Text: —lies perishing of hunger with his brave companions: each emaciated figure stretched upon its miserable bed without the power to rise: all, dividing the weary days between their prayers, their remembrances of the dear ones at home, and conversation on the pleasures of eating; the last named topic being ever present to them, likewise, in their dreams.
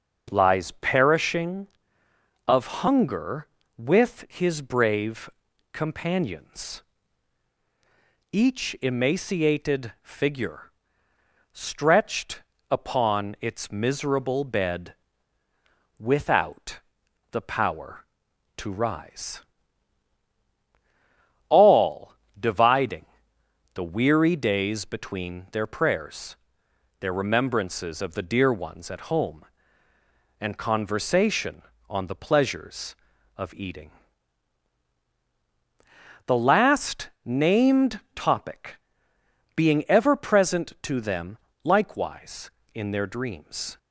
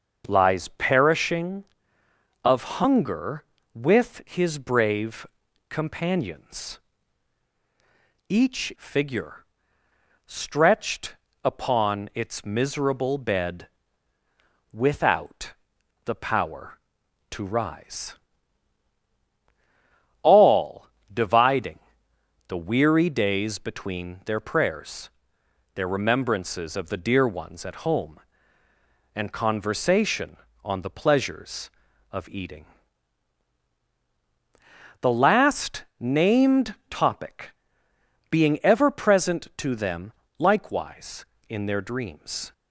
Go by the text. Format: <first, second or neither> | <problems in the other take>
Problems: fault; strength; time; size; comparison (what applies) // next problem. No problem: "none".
first | starts louder than the rest; until 1.2 s; 6.5 dB; also in the first // pauses between "brave" and "companions"; at 5.2 s; 0.44 s long; also in the first // skips "emaciated"; at 8.7 s // pauses between "figure" and "stretched"; noticeable; at 9.4 s; 0.82 s long; noticeable in the first // pauses between "stretched" and "upon"; slight; at 11.1 s; 0.30 s long; slight in the first // pauses between "bed" and "without"; at 13.6 s; 1.0 s long; also in the first // pauses between "without" and "the"; noticeable; at 15.5 s; 0.52 s long; noticeable in the first // pauses between "dividing" and "the"; noticeable; at 21.7 s; 0.70 s long; noticeable in the first // pauses between "named" and "topic"; slight; at 36.7 s; 0.16 s long; slight in the first // pauses between "topic" and "being"; noticeable; at 37.5 s; 0.78 s long; noticeable in the first